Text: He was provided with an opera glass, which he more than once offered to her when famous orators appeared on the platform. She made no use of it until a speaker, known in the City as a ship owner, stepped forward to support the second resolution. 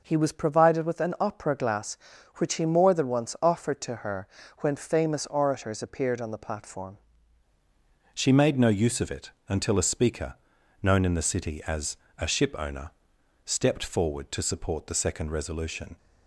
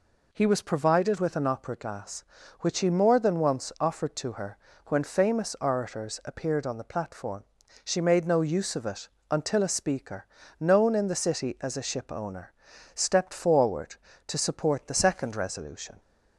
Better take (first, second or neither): second